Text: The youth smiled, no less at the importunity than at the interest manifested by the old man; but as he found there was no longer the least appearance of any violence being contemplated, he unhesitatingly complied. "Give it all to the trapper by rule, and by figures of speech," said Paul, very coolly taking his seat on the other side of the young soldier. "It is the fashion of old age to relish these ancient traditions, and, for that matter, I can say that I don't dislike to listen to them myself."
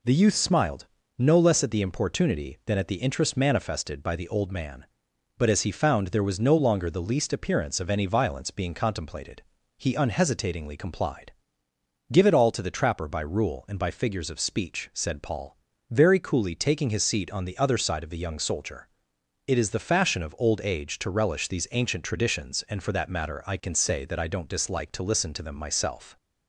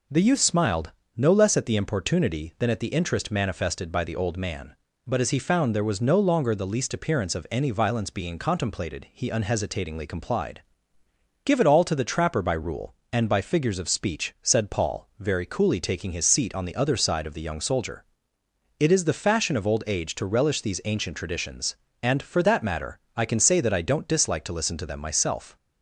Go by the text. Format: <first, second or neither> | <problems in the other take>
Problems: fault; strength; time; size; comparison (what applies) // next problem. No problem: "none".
neither | none